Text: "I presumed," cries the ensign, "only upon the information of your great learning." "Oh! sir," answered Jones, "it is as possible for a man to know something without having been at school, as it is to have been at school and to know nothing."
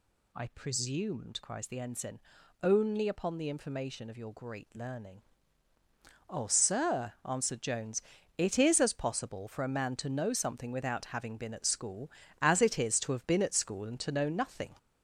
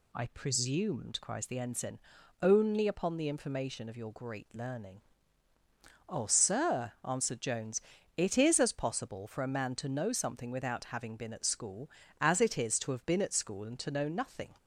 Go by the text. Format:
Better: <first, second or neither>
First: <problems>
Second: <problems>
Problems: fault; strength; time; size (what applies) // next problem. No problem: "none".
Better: second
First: gets louder; noticeable; throughout; 5 dB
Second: none